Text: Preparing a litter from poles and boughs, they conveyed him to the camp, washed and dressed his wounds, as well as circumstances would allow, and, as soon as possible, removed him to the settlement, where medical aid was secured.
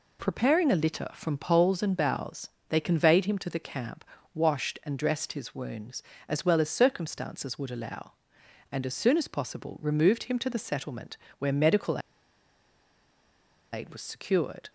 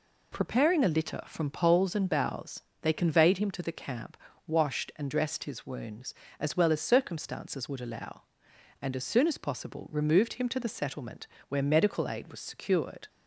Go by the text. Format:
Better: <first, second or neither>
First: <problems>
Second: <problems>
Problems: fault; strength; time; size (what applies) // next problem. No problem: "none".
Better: second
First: pauses between "medical" and "aid"; strong; at 11.9 s; 1.7 s long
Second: none